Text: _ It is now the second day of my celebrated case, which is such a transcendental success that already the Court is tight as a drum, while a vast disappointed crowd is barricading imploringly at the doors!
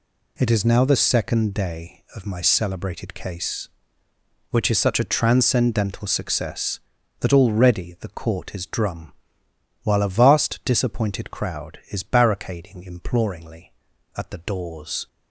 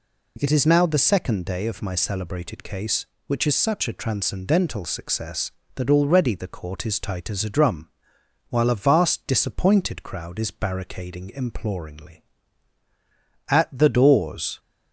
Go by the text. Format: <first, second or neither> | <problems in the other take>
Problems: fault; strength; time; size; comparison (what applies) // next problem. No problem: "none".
second | skips "tight as a"; at 8.6 s